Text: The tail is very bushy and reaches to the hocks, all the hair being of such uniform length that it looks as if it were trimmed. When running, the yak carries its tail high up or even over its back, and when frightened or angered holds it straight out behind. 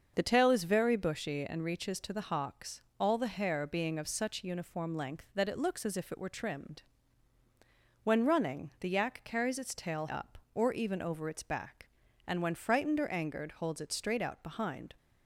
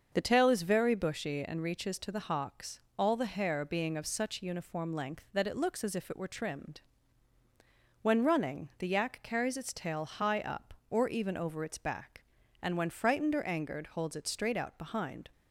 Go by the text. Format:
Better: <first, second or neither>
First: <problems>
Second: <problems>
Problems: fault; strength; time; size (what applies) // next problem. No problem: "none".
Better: second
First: starts louder than the rest; until 1.1 s; 6.5 dB // skips "high"; at 10.0 s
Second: starts louder than the rest; until 1.1 s; 6.5 dB